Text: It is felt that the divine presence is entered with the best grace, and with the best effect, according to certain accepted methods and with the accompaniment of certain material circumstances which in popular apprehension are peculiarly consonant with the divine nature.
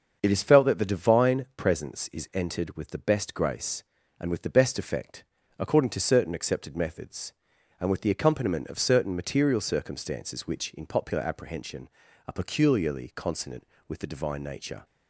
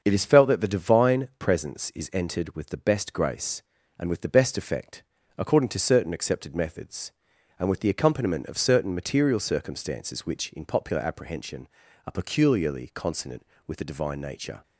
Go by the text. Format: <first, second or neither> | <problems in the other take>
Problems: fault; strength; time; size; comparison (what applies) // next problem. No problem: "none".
neither | starts louder than the rest; the same in both